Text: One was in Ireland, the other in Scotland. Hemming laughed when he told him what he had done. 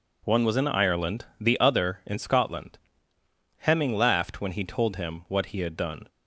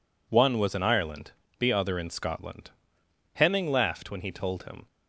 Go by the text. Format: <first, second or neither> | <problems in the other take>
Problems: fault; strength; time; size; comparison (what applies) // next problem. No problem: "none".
first | stops before "what he had done"; at 4.8 s